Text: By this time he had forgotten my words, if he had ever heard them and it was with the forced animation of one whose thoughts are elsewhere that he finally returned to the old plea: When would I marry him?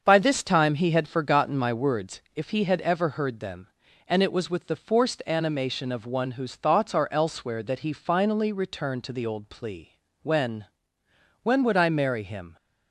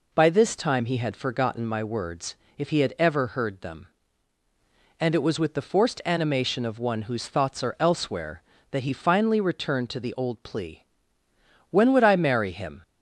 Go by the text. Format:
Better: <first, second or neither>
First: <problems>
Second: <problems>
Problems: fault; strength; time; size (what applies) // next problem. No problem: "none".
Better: second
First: starts louder than the rest; until 1.0 s; 6.5 dB // says "When" twice; at 11.4 s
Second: none